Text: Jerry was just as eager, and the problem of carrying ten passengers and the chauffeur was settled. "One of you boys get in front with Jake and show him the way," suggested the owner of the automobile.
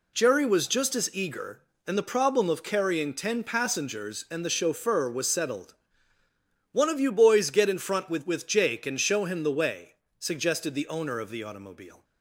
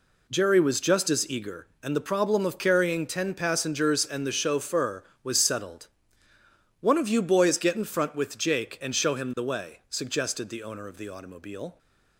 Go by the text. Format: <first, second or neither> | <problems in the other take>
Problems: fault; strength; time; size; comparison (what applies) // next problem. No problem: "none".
second | says "with" twice; at 8.2 s